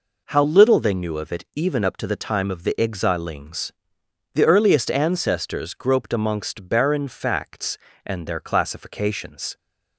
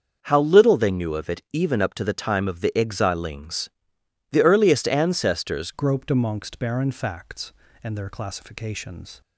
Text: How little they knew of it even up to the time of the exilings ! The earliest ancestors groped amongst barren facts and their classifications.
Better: first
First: none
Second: starts louder than the rest; until 1.2 s; 6.5 dB // changes voice at "groped"; from 5.7 s on; 3.5 s long

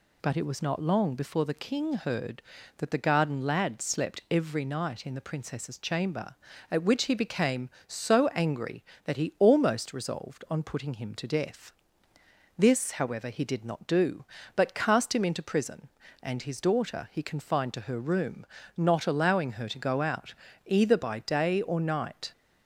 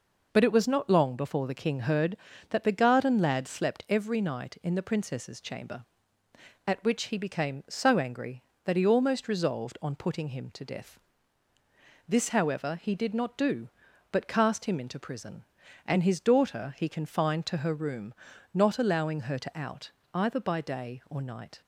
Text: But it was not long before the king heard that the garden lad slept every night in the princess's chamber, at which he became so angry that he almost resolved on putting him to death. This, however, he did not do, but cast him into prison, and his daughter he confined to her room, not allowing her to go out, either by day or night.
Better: first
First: none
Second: skips "go"; at 19.5 s

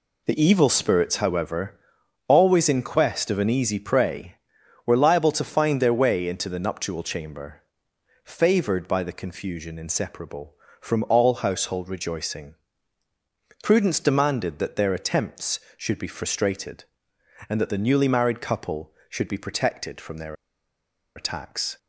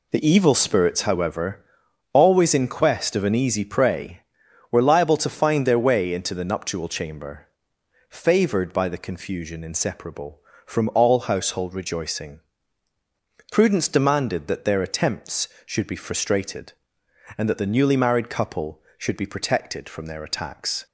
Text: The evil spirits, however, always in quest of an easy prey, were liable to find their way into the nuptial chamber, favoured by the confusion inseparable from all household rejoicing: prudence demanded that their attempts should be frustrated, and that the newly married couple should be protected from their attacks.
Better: second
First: pauses between "their" and "attacks"; noticeable; at 20.3 s; 0.80 s long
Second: none

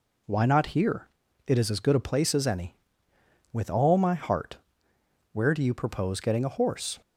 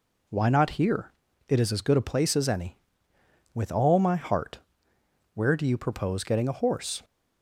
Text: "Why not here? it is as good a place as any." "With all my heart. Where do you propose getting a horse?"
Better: neither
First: none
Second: none

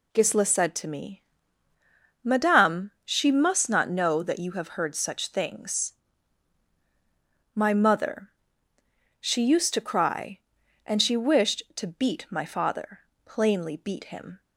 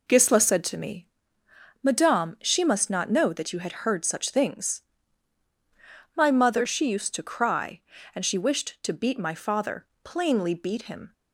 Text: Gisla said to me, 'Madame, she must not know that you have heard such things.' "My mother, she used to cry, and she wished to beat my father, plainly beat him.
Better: first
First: none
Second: says "had" for "have"; at 3.5 s

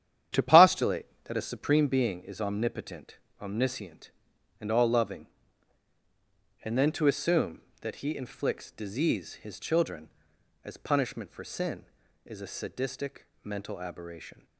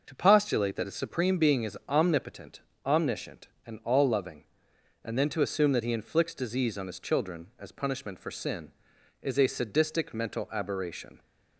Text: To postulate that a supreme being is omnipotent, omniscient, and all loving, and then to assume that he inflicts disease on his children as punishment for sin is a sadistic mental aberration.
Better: second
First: starts louder than the rest; strong; until 1.5 s; 10 dB // skips "on"; at 9.3 s // pauses between "sadistic" and "mental"; slight; at 13.2 s; 0.16 s long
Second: none

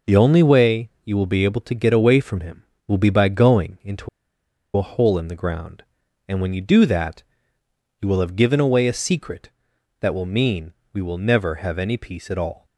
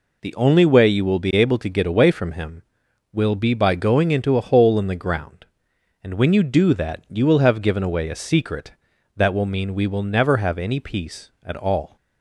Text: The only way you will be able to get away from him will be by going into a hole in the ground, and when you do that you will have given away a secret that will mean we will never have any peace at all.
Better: second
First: pauses between "into" and "a"; noticeable; at 4.0 s; 0.67 s long // pauses between "that" and "you"; noticeable; at 7.2 s; 0.78 s long // pauses between "mean" and "we"; slight; at 10.7 s; 0.20 s long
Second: none

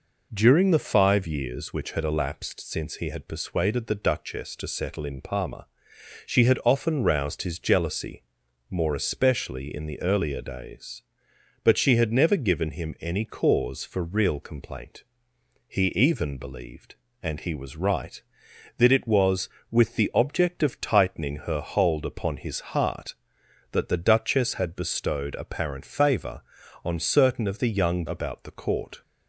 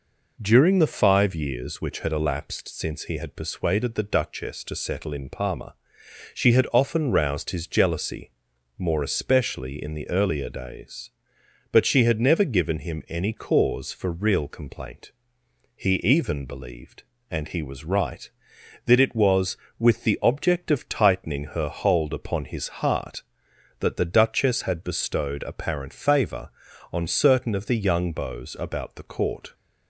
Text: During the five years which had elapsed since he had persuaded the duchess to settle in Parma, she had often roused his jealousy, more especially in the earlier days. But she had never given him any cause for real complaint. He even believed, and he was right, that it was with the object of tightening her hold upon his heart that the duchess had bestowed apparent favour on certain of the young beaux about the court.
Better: second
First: skips "beaux"; at 28.0 s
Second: none

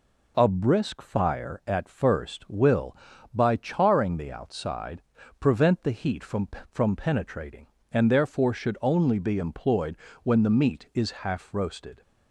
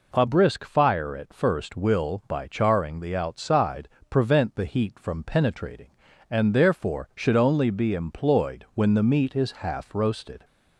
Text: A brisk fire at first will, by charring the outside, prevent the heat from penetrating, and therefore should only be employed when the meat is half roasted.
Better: second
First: says "from" twice; at 6.6 s // pauses between "employed" and "when"; slight; at 9.9 s; 0.28 s long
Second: none

